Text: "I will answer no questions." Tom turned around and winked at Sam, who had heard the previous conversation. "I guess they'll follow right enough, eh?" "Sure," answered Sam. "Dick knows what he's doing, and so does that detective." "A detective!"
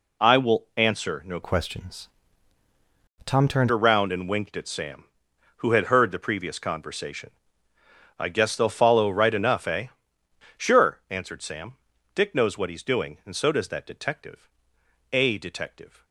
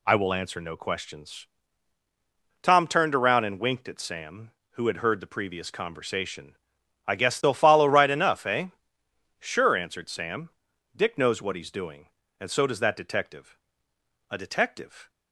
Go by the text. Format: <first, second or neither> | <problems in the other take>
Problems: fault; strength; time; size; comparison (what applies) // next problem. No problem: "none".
second | changes voice from "questions" to "turned"; from 1.4 to 3.6 s; 2.2 s long